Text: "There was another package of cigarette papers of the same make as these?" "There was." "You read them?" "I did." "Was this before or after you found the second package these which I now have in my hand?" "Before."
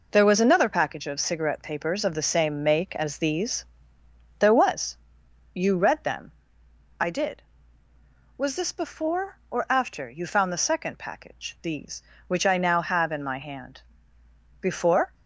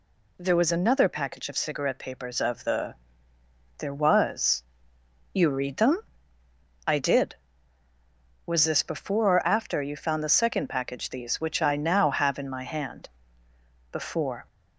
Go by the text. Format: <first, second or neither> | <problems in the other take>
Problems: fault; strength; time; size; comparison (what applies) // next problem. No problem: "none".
first | skips "same make as these"; at 3.3 s